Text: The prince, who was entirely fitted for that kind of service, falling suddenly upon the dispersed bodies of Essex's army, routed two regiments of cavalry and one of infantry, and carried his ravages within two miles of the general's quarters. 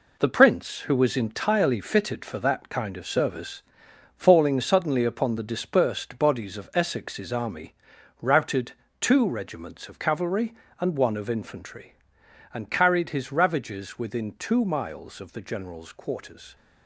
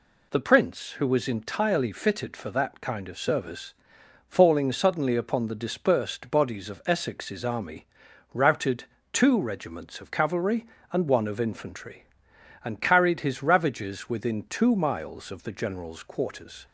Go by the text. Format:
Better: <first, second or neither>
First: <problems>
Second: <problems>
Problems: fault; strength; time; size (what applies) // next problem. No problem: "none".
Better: second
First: gets quieter; strong; throughout; 8 dB // pauses between "routed" and "two"; slight; at 8.7 s; 0.30 s long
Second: pauses between "routed" and "two"; slight; at 8.8 s; 0.30 s long